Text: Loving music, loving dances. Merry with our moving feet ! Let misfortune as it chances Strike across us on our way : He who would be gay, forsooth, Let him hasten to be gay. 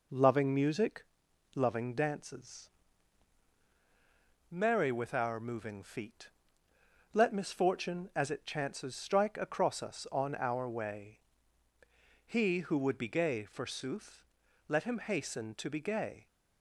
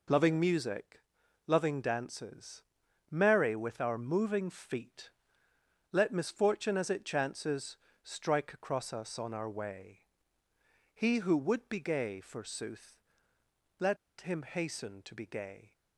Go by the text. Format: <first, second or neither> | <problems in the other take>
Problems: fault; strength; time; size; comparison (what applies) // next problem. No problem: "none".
first | pauses between "chances" and "Strike"; slight; at 7.7 s; 0.26 s long // pauses between "Let" and "him"; slight; at 13.9 s; 0.23 s long